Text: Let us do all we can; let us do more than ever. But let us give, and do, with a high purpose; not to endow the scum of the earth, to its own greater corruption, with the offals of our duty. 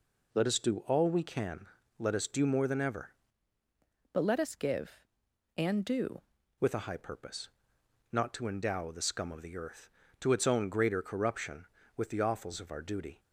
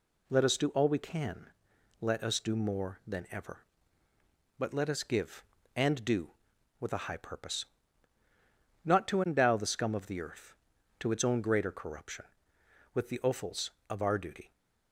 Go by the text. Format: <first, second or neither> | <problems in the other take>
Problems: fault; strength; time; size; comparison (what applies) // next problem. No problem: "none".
second | changes voice from "But" to "do"; from 4.1 to 6.2 s; 2.1 s long